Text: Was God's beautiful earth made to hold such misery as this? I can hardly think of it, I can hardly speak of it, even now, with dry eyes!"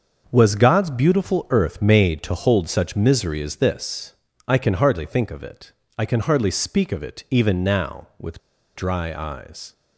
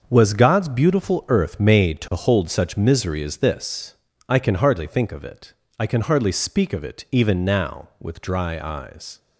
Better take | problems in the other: second | starts louder than the rest; until 1.3 s; 6.5 dB; also in the second // pauses between "with" and "dry"; at 8.3 s; 0.36 s long

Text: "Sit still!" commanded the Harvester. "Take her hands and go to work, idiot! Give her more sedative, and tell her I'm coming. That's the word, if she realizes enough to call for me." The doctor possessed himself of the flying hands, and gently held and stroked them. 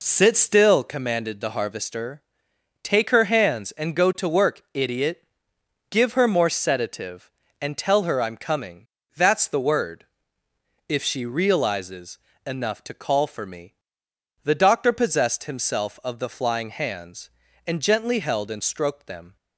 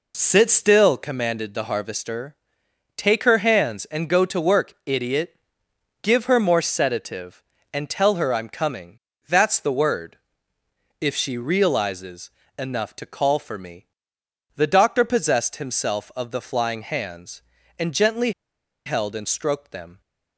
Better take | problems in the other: first | pauses between "realizes" and "enough"; slight; at 12.2 s; 0.28 s long; slight in the first // pauses between "gently" and "held"; noticeable; at 18.3 s; 0.54 s long

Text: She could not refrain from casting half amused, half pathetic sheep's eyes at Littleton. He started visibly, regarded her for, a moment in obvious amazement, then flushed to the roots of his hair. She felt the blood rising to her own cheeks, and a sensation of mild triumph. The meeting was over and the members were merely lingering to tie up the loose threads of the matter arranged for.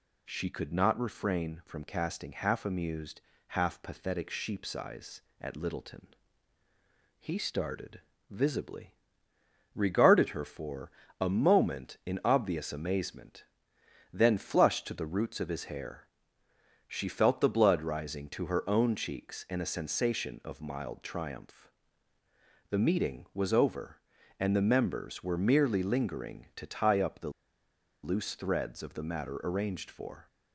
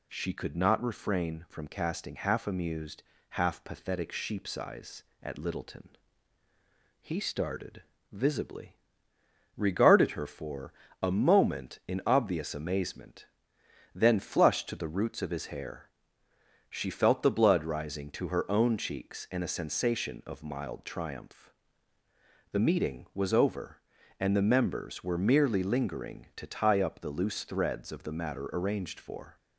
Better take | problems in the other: second | pauses between "started" and "visibly"; slight; at 8.0 s; 0.28 s long; slight in the second // pauses between "the" and "loose"; noticeable; at 27.3 s; 0.72 s long

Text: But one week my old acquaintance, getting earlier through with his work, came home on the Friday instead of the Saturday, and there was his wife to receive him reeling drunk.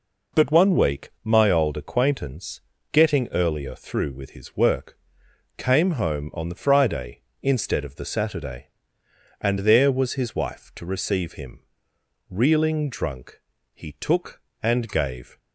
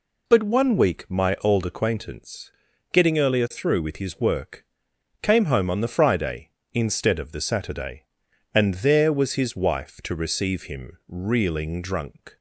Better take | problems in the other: second | pauses between "him" and "reeling"; noticeable; at 11.6 s; 0.66 s long // goes on to say "He took and gave"; from 13.7 s on; 1.6 s long

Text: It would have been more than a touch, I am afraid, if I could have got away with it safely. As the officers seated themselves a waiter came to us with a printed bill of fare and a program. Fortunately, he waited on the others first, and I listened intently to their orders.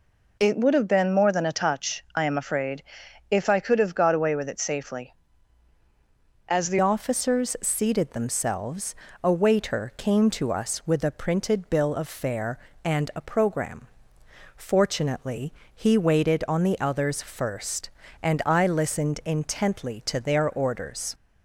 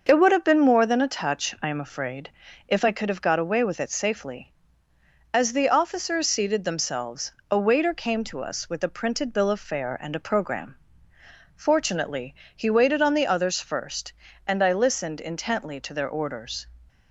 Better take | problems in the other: second | changes voice at "officers"; from 6.7 s on; 14.4 s long // pauses between "themselves" and "a"; slight; at 8.9 s; 0.26 s long; slight in the second

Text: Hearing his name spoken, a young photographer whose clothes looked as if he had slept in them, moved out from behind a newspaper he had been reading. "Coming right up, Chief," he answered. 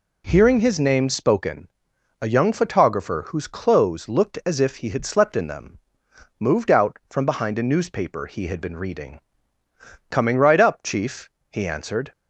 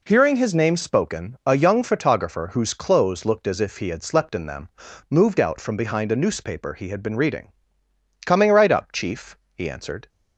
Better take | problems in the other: neither | none

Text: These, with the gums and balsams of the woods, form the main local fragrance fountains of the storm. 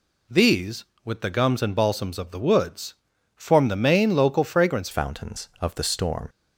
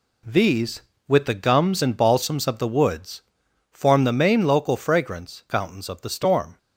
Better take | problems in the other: second | changes voice at "fountains"; from 4.9 s on; 1.3 s long

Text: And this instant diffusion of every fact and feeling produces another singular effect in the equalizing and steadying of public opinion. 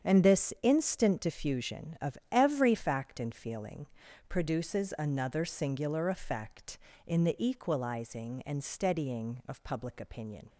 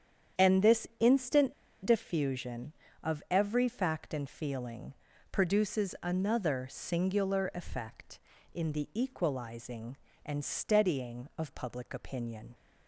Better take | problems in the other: first | starts louder than the rest; strong; until 1.5 s; 8.5 dB; strong in the first // pauses between "instant" and "diffusion"; slight; at 1.5 s; 0.30 s long // pauses between "feeling" and "produces"; slight; at 4.9 s; 0.36 s long; also in the first

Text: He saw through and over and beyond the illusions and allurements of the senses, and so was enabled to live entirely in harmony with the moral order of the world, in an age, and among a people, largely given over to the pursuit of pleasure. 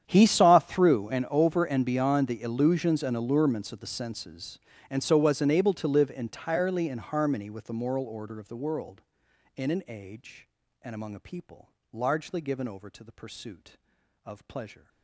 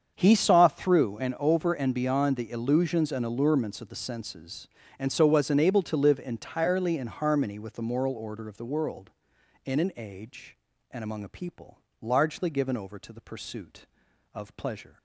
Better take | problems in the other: second | gets quieter; strong; throughout; 23 dB // starts louder than the rest; strong; until 1.0 s; 9 dB; strong in the second

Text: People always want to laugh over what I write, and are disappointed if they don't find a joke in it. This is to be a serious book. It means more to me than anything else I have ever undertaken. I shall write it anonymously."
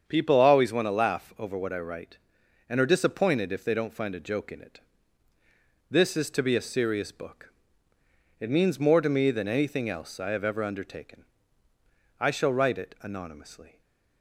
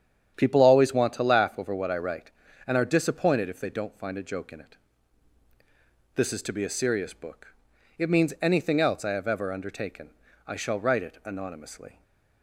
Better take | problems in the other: first | starts louder than the rest; strong; until 1.3 s; 8.5 dB; strong in the first // skips "more to me than"; at 8.3 s // stays silent after the last word; slight; from 11.9 s on; 0.5 s long; slight in the first

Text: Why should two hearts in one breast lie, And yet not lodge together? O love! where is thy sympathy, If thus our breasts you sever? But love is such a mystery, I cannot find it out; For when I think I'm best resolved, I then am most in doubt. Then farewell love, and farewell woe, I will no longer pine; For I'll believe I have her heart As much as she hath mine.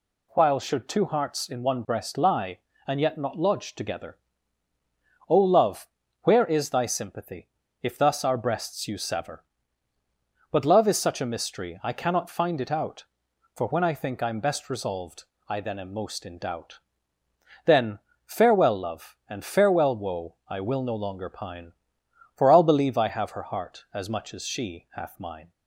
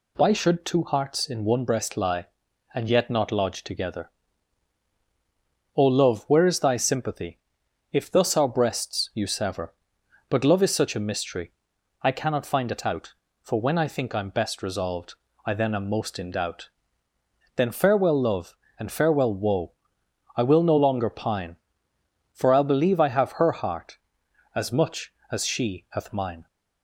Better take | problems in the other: second | says "While" for "Why"; at 0.3 s // pauses between "Then" and "farewell"; slight; at 17.9 s; 0.26 s long

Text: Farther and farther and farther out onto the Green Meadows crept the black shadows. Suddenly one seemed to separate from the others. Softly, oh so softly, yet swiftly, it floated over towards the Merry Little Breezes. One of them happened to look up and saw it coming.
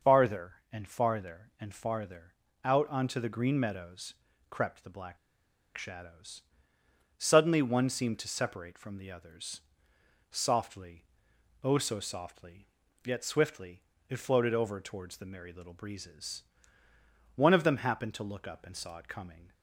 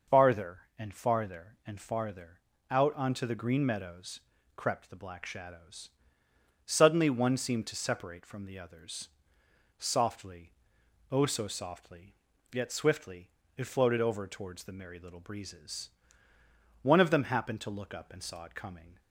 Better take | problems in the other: second | starts louder than the rest; noticeable; until 1.2 s; 6 dB; noticeable in the second // pauses between "farther" and "out"; slight; at 2.3 s; 0.32 s long; slight in the second // pauses between "Meadows" and "crept"; slight; at 4.1 s; 0.36 s long; slight in the second // pauses between "black" and "shadows"; noticeable; at 5.1 s; 0.60 s long

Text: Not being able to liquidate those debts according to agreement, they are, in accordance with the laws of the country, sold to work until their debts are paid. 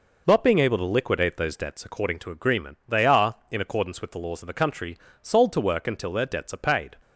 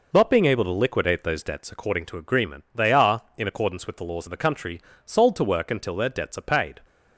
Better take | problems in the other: neither | none

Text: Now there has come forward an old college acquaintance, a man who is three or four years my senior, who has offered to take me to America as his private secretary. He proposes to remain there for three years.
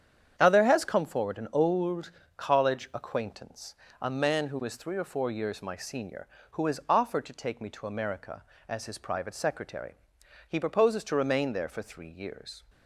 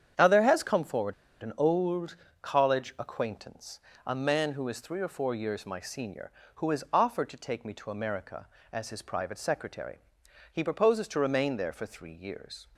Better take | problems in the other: first | starts louder than the rest; strong; until 1.4 s; 8.5 dB; strong in the first // pauses between "forward" and "an"; slight; at 1.1 s; 0.29 s long // pauses between "old" and "college"; slight; at 2.1 s; 0.26 s long; slight in the first

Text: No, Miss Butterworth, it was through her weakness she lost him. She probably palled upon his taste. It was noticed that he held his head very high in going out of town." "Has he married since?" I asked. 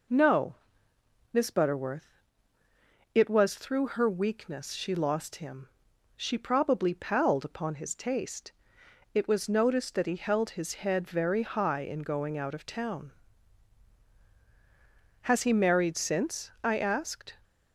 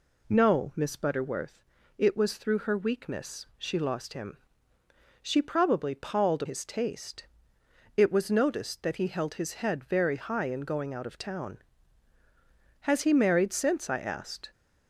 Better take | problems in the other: first | skips "upon"; at 6.4 s

